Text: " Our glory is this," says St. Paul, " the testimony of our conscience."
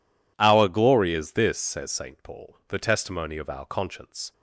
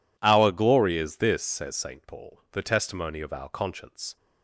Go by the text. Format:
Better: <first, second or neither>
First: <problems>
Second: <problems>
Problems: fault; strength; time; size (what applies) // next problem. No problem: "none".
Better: neither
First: none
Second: none